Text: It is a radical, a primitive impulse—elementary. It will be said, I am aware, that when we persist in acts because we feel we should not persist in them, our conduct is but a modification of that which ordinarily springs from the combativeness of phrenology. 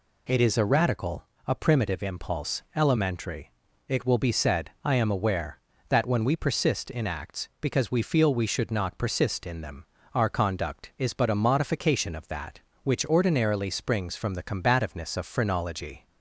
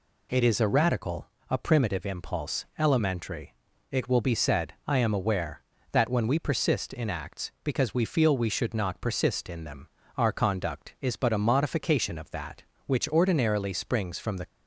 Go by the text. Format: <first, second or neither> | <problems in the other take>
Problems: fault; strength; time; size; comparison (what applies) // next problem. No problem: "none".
first | stops before "combativeness of phrenology"; at 14.4 s